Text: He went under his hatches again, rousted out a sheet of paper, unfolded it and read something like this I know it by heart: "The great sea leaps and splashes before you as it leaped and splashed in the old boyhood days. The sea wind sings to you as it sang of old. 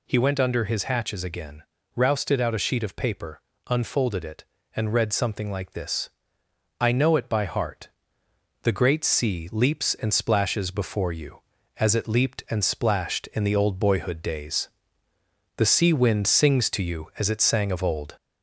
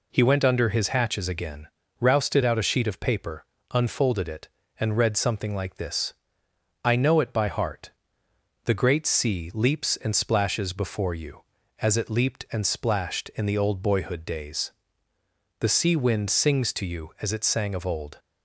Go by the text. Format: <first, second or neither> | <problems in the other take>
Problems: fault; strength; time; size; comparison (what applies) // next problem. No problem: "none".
second | gets louder; slight; throughout; 2 dB // pauses between "this" and "I"; noticeable; at 6.0 s; 0.70 s long; noticeable in the second